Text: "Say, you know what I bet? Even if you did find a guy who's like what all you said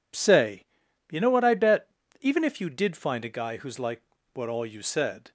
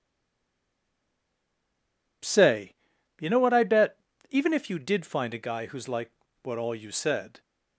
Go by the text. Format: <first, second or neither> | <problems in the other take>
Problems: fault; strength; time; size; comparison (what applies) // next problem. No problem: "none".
first | stays silent before the first word; until 2.2 s; 2.2 s long // pauses between "like" and "what"; slight; at 6.1 s; 0.34 s long; slight in the first